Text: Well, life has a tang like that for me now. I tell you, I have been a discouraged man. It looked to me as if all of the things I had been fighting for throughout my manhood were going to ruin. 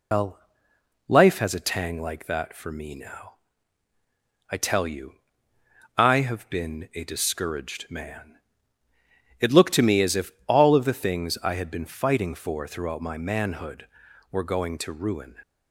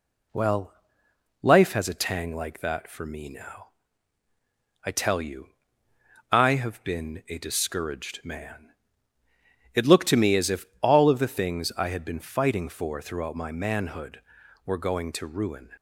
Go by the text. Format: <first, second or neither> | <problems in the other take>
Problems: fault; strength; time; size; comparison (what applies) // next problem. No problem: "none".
second | loses the start of "Well"; at 0.1 s; 135 ms // pauses between "if" and "all"; slight; at 10.3 s; 0.16 s long; slight in the second